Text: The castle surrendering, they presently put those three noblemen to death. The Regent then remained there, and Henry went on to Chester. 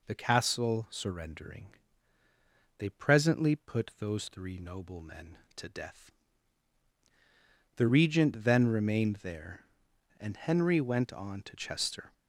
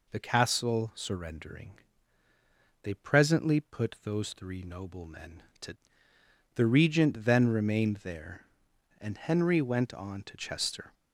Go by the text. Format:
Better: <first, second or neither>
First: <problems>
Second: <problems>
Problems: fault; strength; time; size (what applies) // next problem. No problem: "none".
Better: first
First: none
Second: skips "death"; at 6.1 s